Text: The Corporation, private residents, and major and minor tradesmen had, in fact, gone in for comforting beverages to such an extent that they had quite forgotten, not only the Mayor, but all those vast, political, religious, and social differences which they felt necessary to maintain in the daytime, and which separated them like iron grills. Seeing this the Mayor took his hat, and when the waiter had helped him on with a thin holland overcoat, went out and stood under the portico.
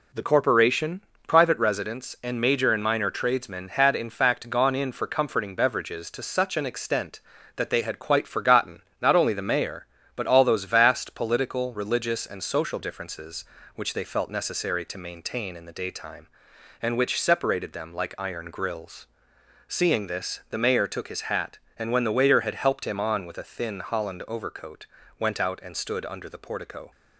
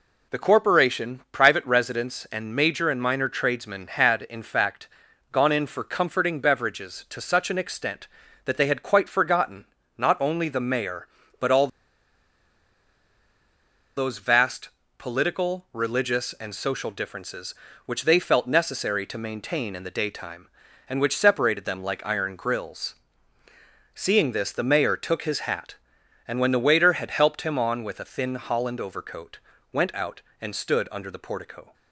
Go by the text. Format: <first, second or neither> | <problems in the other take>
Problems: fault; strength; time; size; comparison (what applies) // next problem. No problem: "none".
first | pauses between "all" and "those"; strong; at 11.6 s; 2.2 s long